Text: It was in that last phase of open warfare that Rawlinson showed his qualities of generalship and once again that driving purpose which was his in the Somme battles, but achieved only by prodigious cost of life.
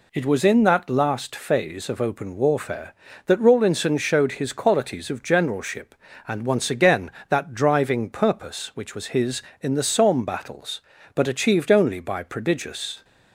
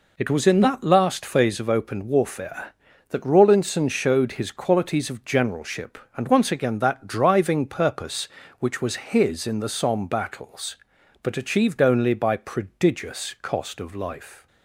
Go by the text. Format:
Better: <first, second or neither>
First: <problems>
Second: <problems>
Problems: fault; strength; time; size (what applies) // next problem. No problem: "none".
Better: second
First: stops before "cost of life"; at 13.0 s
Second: none